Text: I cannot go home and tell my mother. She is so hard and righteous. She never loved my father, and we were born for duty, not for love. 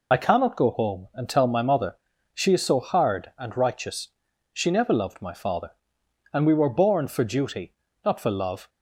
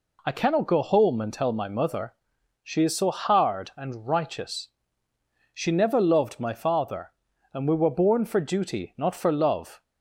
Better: second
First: loses the start of "I"; at 0.1 s; 40 ms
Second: none

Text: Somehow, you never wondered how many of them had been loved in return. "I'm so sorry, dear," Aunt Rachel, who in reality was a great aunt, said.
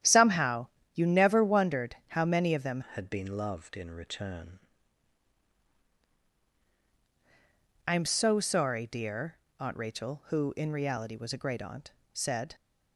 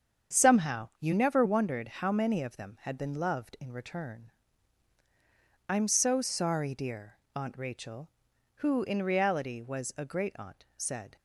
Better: second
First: starts louder than the rest; strong; until 1.3 s; 10.5 dB // changes voice from "had" to "return"; from 2.9 to 4.5 s; 1.6 s long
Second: starts louder than the rest; strong; until 1.4 s; 7.5 dB

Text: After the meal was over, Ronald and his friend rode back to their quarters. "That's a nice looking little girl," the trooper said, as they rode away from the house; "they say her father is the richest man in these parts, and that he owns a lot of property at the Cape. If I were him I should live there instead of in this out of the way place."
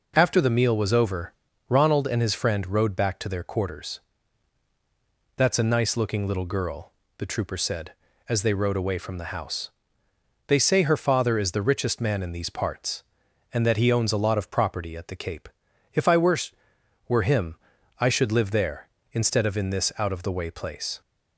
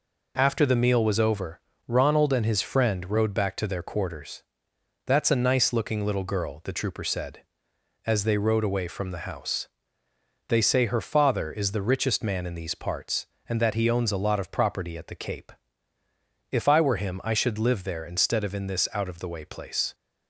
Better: second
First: says "were" twice; at 17.0 s // pauses between "him" and "I"; at 17.5 s; 0.42 s long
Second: none

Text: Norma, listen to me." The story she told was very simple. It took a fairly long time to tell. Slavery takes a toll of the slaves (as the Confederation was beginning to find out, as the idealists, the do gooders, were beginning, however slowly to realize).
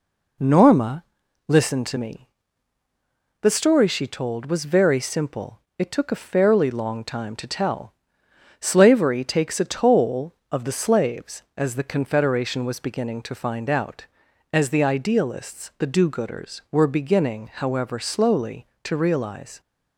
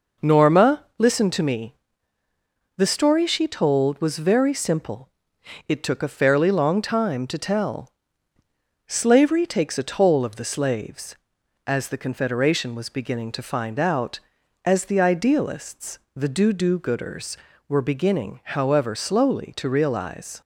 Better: first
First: none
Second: says "do" twice; at 16.5 s

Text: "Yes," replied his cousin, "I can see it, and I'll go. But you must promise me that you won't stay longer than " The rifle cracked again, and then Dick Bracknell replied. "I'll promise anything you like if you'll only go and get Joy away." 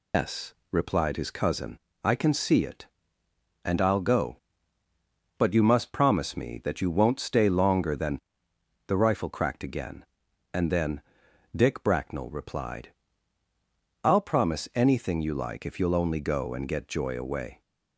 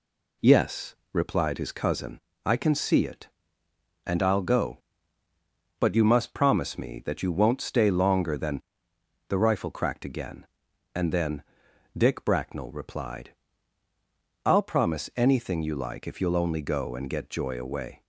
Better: second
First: loses the start of "Yes"; at 0.1 s; 155 ms // pauses between "then" and "Dick"; noticeable; at 11.0 s; 0.54 s long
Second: pauses between "then" and "Dick"; noticeable; at 11.4 s; 0.54 s long

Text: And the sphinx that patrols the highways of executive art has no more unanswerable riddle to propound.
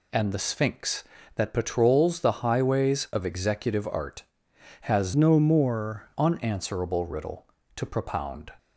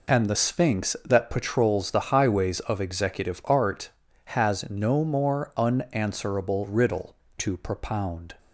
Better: second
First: changes voice from "no" to "more"; from 5.1 to 6.0 s; 0.9 s long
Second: none

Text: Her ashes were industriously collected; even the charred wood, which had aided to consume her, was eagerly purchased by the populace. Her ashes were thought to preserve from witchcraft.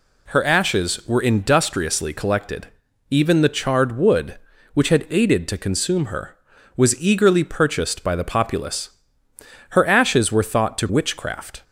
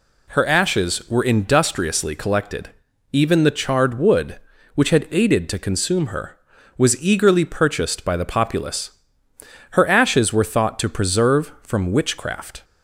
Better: second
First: skips "preserve from"; at 10.8 s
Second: none

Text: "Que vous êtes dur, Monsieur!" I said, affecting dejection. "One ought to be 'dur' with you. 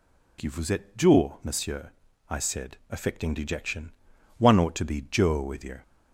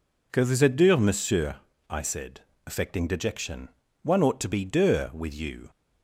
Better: neither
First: none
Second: none

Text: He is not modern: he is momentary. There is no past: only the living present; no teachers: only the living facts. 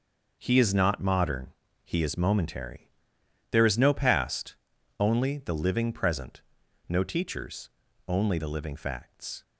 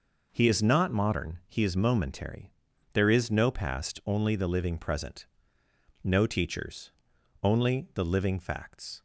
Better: neither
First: none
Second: none

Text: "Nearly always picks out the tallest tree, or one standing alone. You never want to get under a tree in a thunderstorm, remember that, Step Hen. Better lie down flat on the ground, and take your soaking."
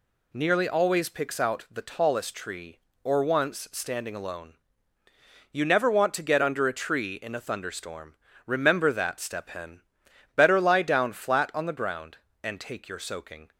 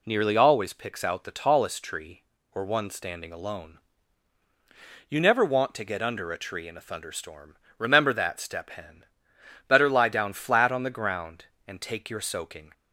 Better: second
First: says "once" for "one"; at 3.2 s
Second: none

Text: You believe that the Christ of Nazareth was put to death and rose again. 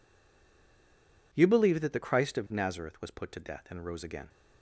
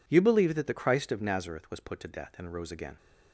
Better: second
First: stays silent before the first word; noticeable; until 1.3 s; 1.3 s long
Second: none

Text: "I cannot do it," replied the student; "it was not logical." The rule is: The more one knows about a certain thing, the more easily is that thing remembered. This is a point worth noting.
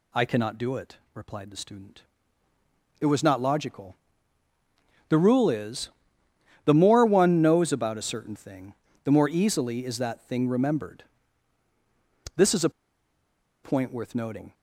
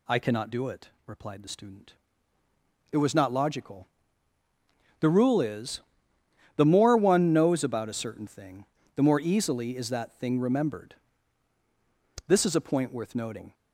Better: second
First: pauses between "a" and "point"; noticeable; at 12.7 s; 0.93 s long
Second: none

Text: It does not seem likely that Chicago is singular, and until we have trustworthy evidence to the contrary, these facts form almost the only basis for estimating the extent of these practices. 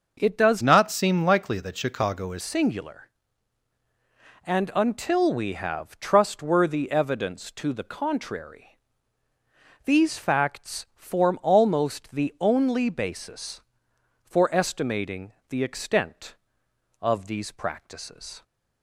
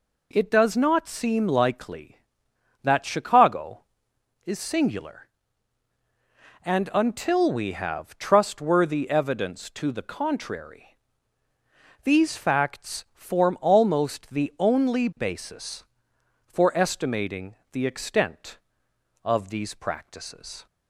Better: second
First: changes voice from "not" to "is"; from 0.6 to 2.4 s; 1.8 s long // pauses between "estimating" and "the"; slight; at 15.3 s; 0.18 s long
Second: pauses between "estimating" and "the"; slight; at 17.5 s; 0.18 s long

